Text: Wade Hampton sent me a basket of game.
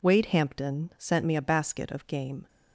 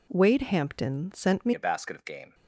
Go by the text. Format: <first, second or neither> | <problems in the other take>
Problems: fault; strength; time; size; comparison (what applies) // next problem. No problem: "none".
first | changes voice at "a"; from 1.5 s on; 0.8 s long